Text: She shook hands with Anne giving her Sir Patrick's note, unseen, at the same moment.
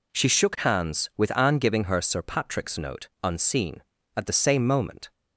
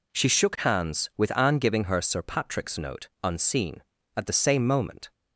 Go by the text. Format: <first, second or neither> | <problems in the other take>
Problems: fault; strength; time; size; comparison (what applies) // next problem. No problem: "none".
neither | none